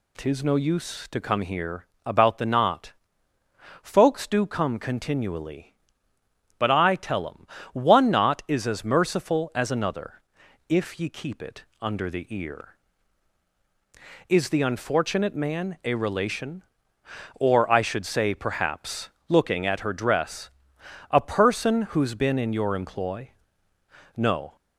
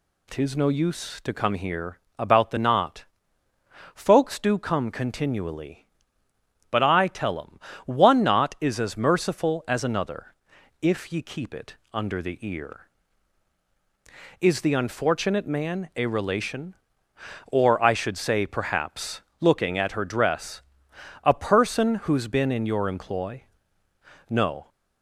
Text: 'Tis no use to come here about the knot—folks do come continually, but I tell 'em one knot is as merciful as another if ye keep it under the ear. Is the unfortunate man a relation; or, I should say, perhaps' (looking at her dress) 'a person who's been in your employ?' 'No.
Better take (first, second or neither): neither